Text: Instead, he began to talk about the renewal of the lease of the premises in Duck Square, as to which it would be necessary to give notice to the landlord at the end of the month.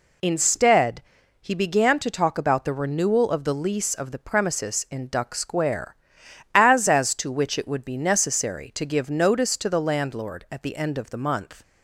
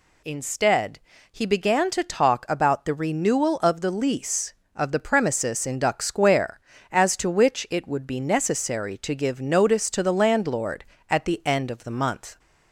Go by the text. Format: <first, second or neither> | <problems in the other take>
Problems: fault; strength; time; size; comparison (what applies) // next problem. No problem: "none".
second | says "as" twice; at 6.8 s